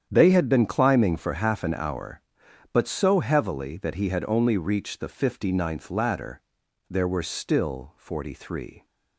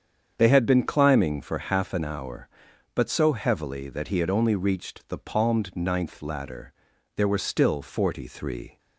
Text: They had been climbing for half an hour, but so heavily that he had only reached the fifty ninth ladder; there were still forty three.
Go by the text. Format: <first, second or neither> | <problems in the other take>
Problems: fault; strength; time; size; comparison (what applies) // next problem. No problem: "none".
first | starts louder than the rest; strong; until 1.3 s; 7.5 dB; strong in the first // says "palmed" for "fifty"; at 5.1 s